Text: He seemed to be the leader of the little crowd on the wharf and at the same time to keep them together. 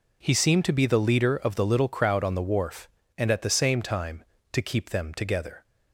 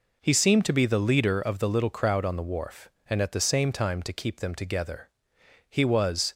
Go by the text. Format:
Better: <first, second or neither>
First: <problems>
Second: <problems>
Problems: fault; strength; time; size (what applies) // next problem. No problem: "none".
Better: first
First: none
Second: goes on to say "He was"; noticeable; from 5.6 s on; 0.64 s long